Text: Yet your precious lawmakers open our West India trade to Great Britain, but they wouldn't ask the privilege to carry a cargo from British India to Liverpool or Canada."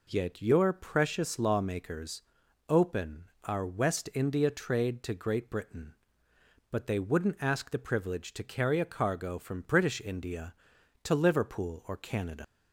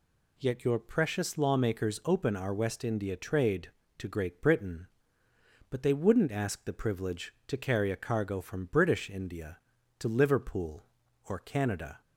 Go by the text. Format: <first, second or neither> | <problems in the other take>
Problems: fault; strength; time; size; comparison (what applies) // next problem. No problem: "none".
second | pauses between "lawmakers" and "open"; at 2.2 s; 0.44 s long // pauses between "open" and "our"; slight; at 3.2 s; 0.20 s long // leaves "Canada" unfinished; at 12.4 s; 95 ms